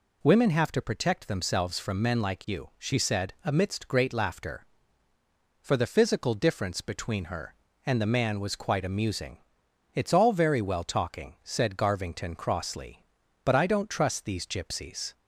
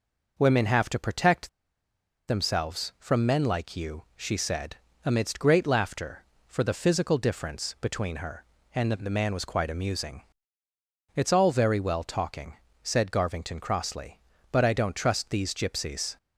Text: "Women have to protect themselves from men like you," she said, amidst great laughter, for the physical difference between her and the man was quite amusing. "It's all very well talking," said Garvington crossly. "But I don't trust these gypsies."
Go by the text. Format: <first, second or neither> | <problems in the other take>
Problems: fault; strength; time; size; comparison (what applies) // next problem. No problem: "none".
first | pauses between "protect" and "themselves"; noticeable; at 1.4 s; 0.79 s long